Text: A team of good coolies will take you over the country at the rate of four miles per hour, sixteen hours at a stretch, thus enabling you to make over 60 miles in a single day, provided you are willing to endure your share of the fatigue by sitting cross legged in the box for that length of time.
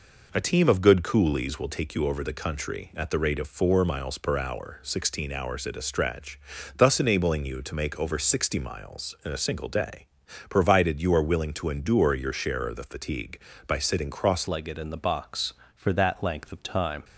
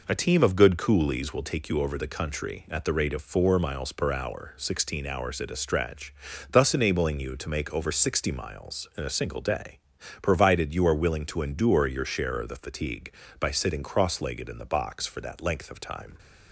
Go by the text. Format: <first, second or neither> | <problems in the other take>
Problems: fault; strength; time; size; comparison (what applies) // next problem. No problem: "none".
second | changes voice at "legged"; from 14.4 s on; 2.6 s long